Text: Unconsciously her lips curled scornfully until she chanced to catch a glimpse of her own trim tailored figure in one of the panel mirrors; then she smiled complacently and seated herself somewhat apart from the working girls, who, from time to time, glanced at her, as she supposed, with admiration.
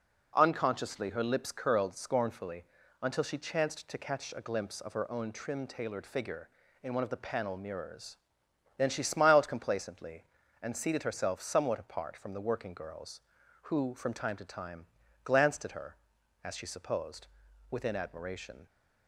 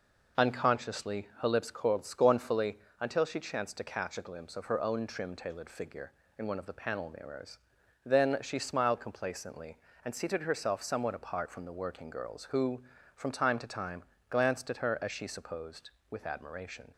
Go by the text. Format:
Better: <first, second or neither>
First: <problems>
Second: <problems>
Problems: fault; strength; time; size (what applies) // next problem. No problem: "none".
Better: second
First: pauses between "scornfully" and "until"; at 2.6 s; 0.38 s long // says "within" for "with"; at 17.6 s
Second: pauses between "scornfully" and "until"; slight; at 2.7 s; 0.22 s long